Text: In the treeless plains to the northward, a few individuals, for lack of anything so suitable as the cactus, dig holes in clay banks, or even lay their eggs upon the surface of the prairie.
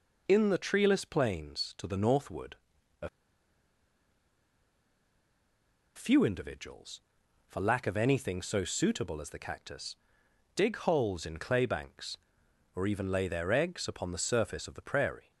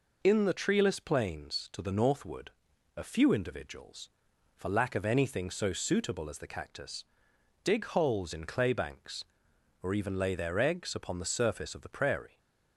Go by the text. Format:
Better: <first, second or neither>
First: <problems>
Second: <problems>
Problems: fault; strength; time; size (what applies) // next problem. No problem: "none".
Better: second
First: pauses between "a" and "few"; strong; at 3.0 s; 2.8 s long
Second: none